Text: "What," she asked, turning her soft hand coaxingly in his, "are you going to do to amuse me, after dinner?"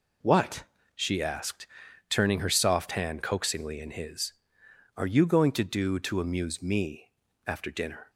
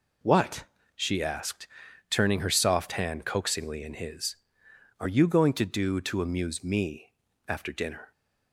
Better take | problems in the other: neither | none

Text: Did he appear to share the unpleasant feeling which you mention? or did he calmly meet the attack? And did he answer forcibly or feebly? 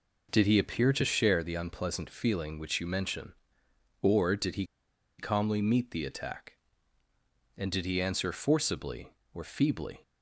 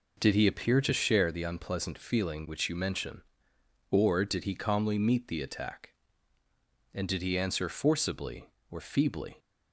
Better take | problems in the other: second | pauses between "he" and "calmly"; noticeable; at 4.6 s; 0.54 s long

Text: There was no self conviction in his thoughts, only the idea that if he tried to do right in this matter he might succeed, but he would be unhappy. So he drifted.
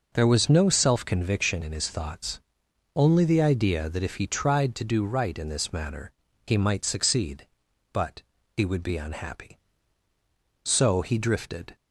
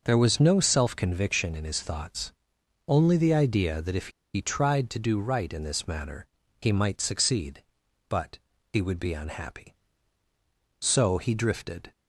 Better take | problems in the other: first | pauses between "if" and "he"; slight; at 4.0 s; 0.25 s long // pauses between "matter" and "he"; slight; at 6.2 s; 0.34 s long; slight in the first // pauses between "but" and "he"; slight; at 8.3 s; 0.34 s long; slight in the first

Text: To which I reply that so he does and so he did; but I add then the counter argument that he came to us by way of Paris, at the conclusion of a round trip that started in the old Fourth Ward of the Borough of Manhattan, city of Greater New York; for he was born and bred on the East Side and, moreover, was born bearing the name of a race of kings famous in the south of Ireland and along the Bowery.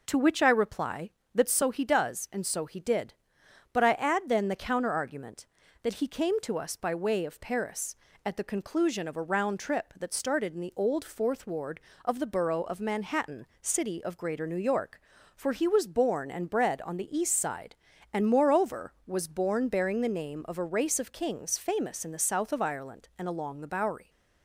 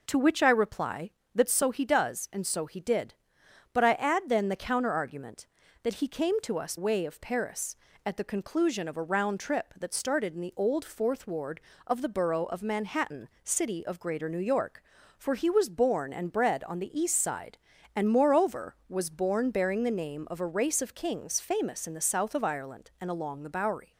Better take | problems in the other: first | skips "by"; at 6.7 s

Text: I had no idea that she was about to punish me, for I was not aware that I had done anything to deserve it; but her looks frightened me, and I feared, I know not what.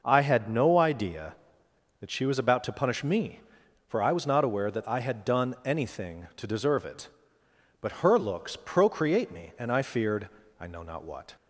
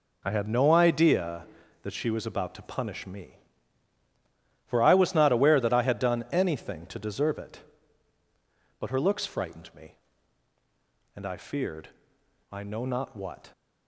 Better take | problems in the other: second | says "procreate" for "frightened"; at 8.5 s

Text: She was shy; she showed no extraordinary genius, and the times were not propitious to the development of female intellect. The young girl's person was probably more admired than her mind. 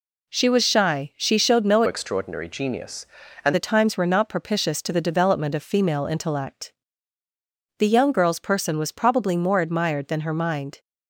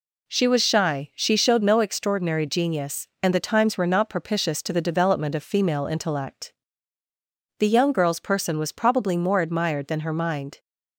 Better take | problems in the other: second | changes voice from "extraordinary" to "and"; from 1.8 to 3.5 s; 1.7 s long

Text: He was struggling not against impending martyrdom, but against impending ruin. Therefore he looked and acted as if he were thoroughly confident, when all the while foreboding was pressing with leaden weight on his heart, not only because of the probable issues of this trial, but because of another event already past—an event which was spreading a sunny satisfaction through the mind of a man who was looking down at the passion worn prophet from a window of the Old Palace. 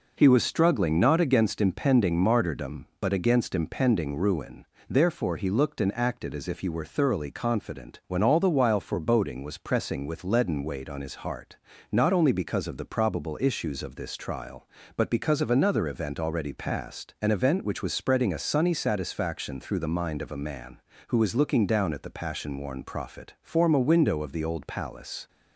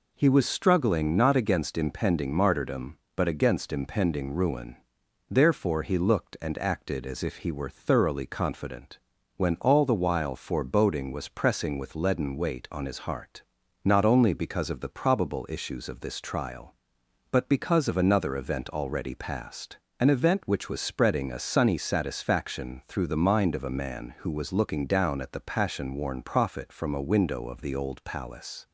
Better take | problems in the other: second | says "form" for "from"; at 23.4 s

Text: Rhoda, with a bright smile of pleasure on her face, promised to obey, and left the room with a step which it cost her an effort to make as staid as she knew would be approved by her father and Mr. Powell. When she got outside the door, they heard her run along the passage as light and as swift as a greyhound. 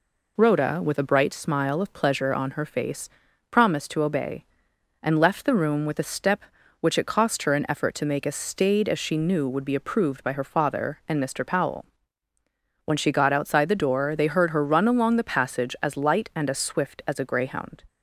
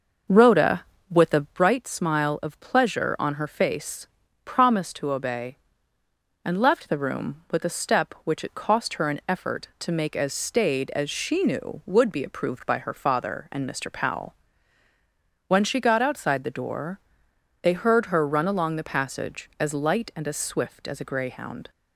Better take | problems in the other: first | starts louder than the rest; noticeable; until 1.6 s; 6 dB

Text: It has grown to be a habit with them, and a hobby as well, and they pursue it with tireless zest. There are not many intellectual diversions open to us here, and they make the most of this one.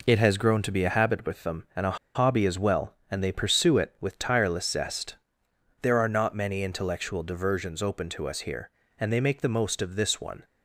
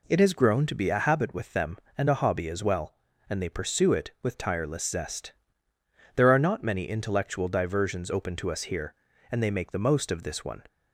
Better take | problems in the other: second | pauses between "a" and "hobby"; slight; at 1.9 s; 0.18 s long

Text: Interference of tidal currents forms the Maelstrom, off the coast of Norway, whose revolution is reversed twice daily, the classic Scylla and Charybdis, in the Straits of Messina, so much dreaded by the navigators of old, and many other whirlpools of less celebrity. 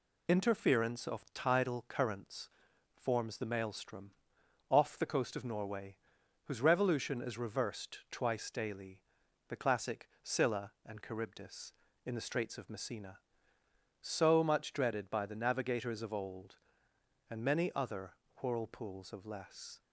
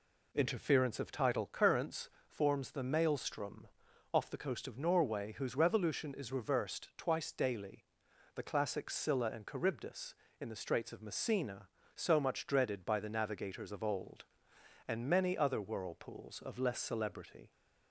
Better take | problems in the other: second | pauses between "currents" and "forms"; noticeable; at 2.4 s; 0.46 s long; slight in the second // pauses between "other" and "whirlpools"; slight; at 18.1 s; 0.30 s long // stops before "celebrity"; at 19.8 s

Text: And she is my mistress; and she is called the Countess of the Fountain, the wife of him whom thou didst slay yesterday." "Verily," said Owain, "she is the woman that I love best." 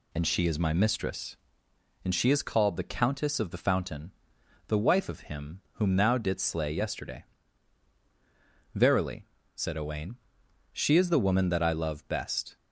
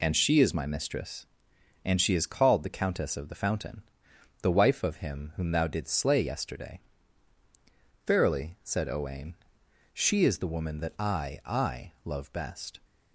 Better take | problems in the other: first | says "I" twice; at 11.4 s

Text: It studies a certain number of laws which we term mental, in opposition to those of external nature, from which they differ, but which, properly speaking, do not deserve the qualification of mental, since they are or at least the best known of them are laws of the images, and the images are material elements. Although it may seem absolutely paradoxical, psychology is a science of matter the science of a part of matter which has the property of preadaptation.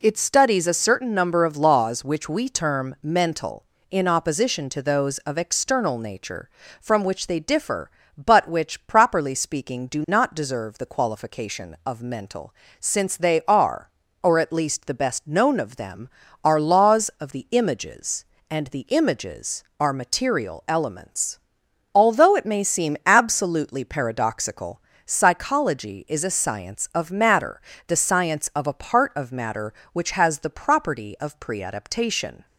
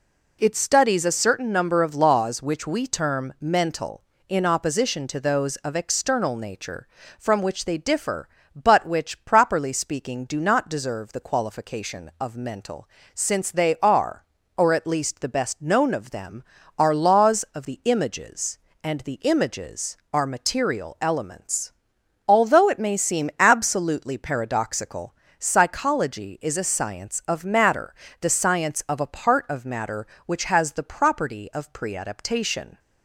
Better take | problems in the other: neither | pauses between "matter" and "the"; slight; the same in both

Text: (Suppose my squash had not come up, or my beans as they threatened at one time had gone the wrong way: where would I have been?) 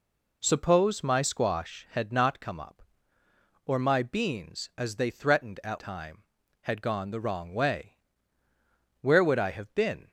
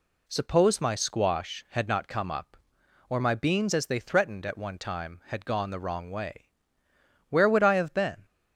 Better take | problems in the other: second | skips "one"; at 5.7 s

